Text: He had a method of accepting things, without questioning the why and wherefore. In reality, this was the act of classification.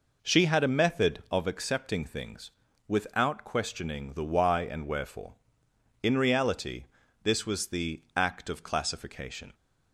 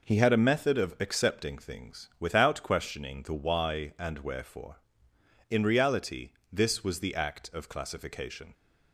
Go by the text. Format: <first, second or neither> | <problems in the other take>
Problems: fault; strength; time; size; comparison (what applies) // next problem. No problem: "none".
second | says "She" for "He"; at 0.2 s